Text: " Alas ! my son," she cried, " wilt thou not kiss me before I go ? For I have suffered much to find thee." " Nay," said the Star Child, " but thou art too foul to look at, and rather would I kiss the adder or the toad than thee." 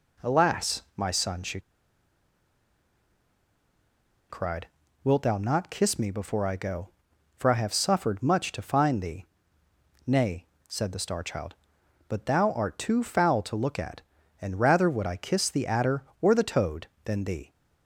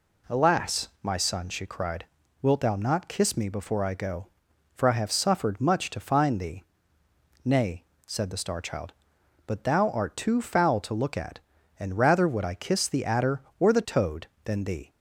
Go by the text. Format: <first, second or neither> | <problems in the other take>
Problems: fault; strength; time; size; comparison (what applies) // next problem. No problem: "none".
second | pauses between "she" and "cried"; strong; at 1.6 s; 2.6 s long